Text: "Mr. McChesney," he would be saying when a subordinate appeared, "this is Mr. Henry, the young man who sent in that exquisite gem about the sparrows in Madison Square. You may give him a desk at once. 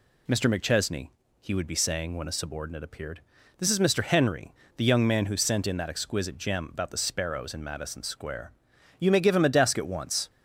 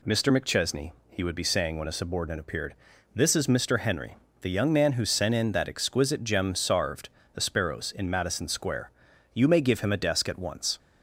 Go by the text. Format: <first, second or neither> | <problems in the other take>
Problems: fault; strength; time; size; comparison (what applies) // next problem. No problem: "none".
first | says "sarved" for "about"; at 6.5 s